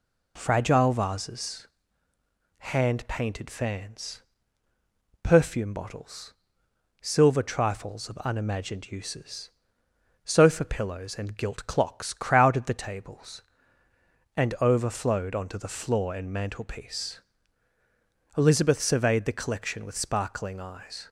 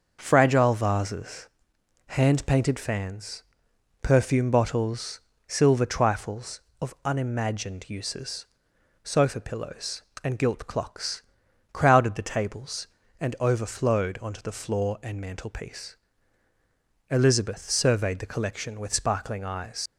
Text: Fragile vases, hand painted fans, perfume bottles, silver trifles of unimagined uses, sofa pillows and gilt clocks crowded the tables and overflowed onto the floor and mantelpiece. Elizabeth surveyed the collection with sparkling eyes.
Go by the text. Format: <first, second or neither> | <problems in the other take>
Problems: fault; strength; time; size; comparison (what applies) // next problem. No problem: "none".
first | starts louder than the rest; until 1.2 s; 6.5 dB // pauses between "clocks" and "crowded"; noticeable; at 11.2 s; 0.48 s long // leaves "eyes" unfinished; at 19.8 s; 100 ms